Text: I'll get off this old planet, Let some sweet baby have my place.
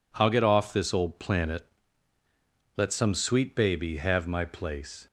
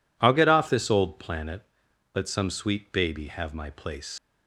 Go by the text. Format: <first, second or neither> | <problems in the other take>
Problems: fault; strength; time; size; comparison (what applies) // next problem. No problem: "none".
first | leaves "place" unfinished; at 4.1 s; 95 ms